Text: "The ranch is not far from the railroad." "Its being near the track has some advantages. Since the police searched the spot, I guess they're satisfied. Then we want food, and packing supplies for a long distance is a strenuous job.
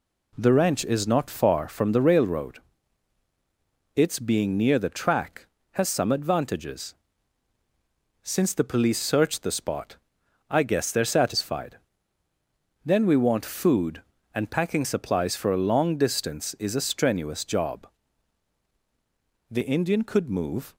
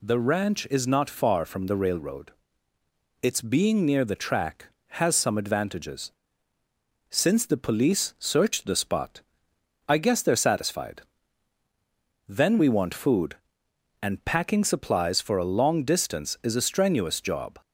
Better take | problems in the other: second | goes on to say "The Indian could move"; noticeable; from 19.5 s on; 1.2 s long

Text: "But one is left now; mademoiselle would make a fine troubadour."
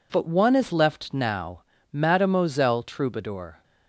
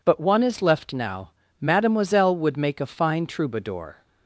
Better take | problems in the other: second | skips "would make a fine"; at 2.8 s

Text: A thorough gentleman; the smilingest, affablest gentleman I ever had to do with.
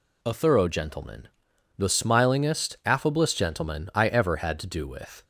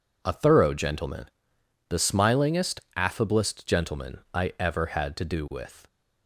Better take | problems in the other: neither | none

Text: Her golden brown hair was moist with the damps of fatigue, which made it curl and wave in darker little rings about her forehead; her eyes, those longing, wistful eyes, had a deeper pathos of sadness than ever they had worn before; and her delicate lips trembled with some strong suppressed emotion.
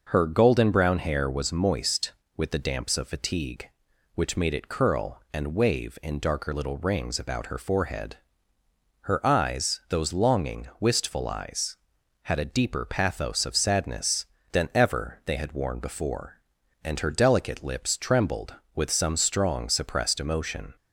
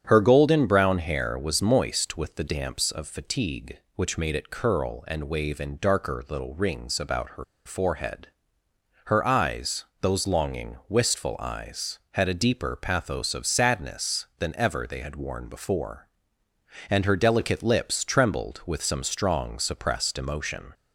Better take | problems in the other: first | starts louder than the rest; strong; until 1.0 s; 8.5 dB // pauses between "her" and "forehead"; slight; at 7.4 s; 0.22 s long

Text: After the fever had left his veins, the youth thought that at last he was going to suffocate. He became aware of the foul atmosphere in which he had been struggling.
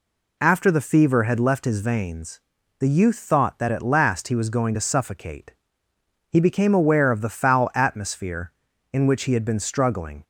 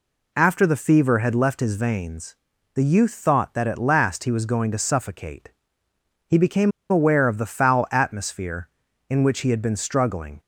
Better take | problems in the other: first | pauses between "became" and "aware"; slight; at 6.7 s; 0.19 s long

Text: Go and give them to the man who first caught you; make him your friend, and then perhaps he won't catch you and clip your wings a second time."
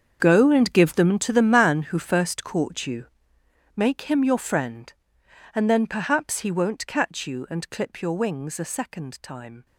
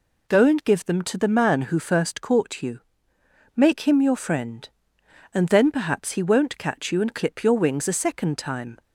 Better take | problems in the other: second | gets quieter; strong; throughout; 14.5 dB

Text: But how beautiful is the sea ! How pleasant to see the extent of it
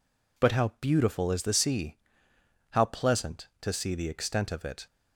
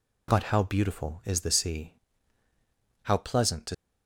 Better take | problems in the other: first | stops before "see the extent of it"; at 3.7 s

